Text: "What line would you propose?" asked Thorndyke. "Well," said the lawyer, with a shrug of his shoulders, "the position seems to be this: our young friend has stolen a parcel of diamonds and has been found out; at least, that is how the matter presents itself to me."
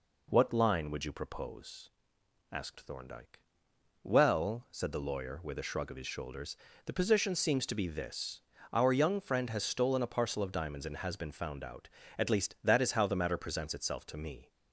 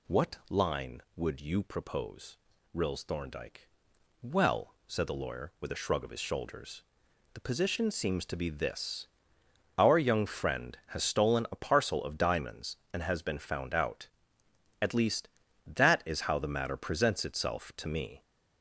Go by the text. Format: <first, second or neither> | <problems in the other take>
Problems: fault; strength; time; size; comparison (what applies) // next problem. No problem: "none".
first | says "rills" for "asked"; at 2.7 s